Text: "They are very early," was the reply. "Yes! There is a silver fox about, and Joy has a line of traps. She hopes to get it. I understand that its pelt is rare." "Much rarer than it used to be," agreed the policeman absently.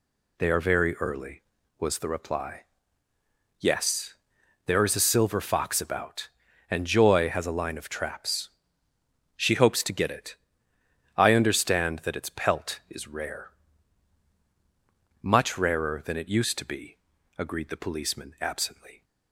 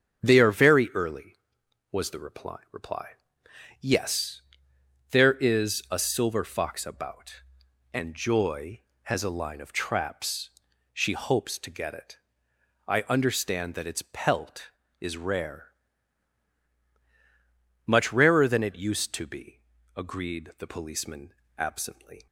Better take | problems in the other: first | starts louder than the rest; strong; until 1.2 s; 8.5 dB // says "reply" twice; at 2.7 s // pauses between "policeman" and "absently"; slight; at 21.3 s; 0.24 s long

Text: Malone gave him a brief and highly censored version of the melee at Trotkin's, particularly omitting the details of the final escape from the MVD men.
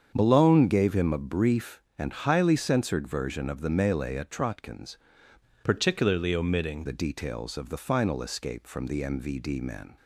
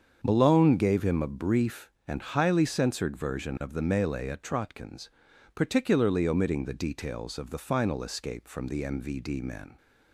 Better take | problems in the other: second | starts louder than the rest; strong; until 1.1 s; 7.5 dB; strong in the second // changes voice from "particularly" to "omitting"; from 5.6 to 6.8 s; 1.2 s long

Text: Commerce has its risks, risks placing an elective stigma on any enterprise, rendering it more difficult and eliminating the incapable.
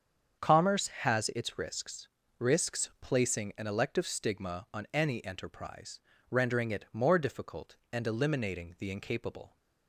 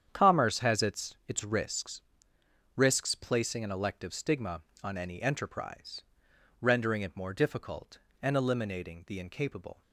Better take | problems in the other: first | starts louder than the rest; strong; until 1.1 s; 8.5 dB; strong in the first // says "its" twice; at 1.2 s

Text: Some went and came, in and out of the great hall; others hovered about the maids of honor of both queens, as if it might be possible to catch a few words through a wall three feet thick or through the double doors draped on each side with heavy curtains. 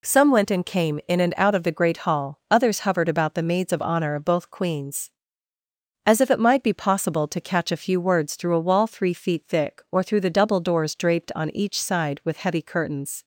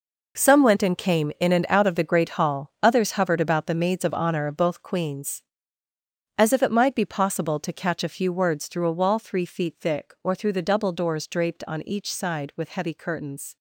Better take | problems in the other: first | gets quieter; strong; throughout; 12 dB

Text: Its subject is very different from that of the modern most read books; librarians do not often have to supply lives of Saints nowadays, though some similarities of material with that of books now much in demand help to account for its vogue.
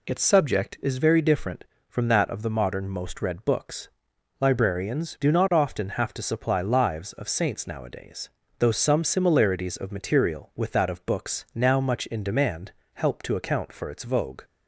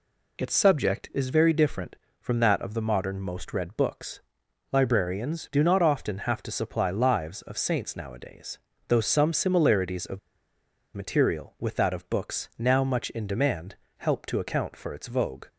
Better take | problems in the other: first | pauses between "of" and "material"; noticeable; at 10.1 s; 0.77 s long // pauses between "demand" and "help"; slight; at 13.7 s; 0.22 s long; slight in the first

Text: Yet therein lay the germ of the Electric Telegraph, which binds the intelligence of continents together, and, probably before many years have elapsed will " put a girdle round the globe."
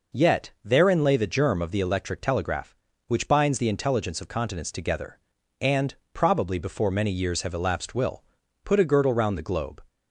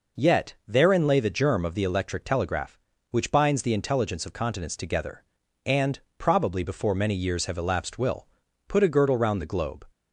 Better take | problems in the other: neither | none

